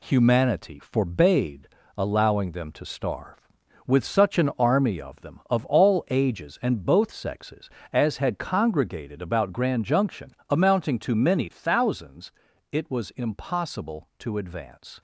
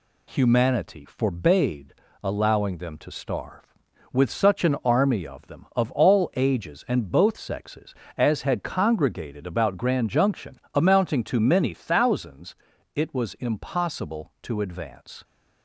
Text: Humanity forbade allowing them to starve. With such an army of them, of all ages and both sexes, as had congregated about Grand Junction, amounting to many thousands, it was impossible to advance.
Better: second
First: gets quieter; throughout; 6.5 dB // pauses between "forbade" and "allowing"; slight; at 1.6 s; 0.28 s long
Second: pauses between "forbade" and "allowing"; slight; at 1.9 s; 0.28 s long

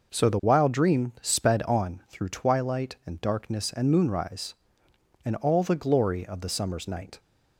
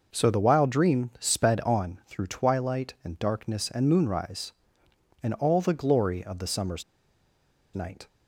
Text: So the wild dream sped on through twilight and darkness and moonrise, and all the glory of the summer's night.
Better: first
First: none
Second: pauses between "summer's" and "night"; noticeable; at 6.8 s; 0.90 s long

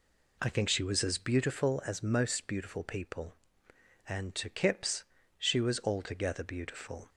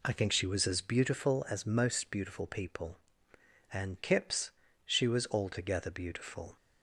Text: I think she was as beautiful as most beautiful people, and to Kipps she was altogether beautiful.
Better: first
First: pauses between "Kipps" and "she"; slight; at 5.0 s; 0.34 s long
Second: skips "to"; at 3.9 s // pauses between "Kipps" and "she"; slight; at 4.5 s; 0.34 s long

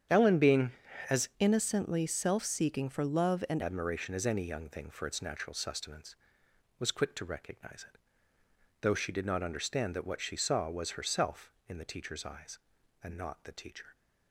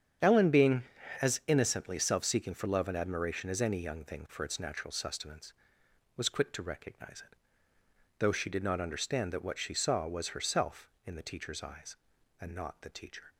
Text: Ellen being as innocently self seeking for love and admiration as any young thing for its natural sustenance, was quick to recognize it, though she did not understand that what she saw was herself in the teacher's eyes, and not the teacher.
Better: second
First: starts louder than the rest; strong; until 1.6 s; 9 dB // changes voice from "innocently" to "and"; from 1.3 to 3.6 s; 2.3 s long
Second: starts louder than the rest; strong; until 1.6 s; 8.5 dB

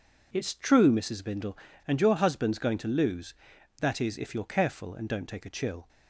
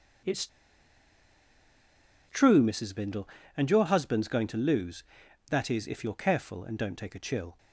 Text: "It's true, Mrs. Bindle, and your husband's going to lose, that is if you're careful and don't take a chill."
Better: first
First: none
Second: pauses between "It's" and "true"; strong; at 0.4 s; 1.8 s long

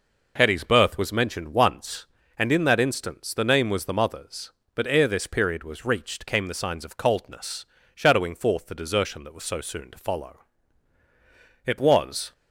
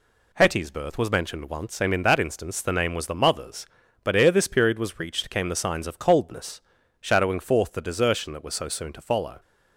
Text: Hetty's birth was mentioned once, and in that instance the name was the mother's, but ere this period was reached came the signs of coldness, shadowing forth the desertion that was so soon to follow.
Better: second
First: goes on to say "It was"; noticeable; from 11.6 s on; 0.68 s long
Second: none

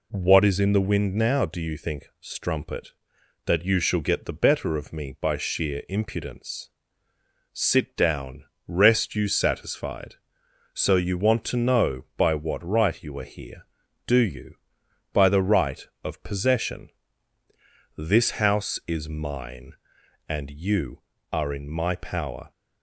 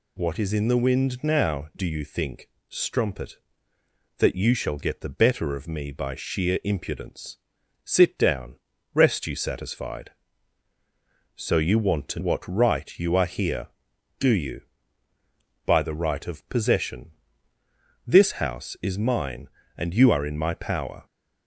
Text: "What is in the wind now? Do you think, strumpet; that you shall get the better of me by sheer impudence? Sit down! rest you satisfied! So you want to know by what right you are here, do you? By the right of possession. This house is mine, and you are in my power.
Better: first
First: none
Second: skips "know by"; at 12.1 s

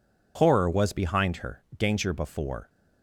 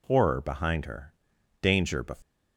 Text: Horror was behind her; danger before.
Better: first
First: none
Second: skips "was"; at 0.4 s

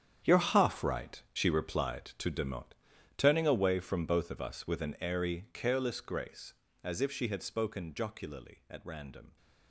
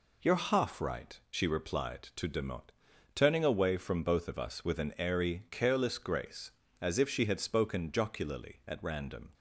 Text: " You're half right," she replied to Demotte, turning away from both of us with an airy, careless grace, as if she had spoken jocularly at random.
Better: second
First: gets quieter; strong; throughout; 14.5 dB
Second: none

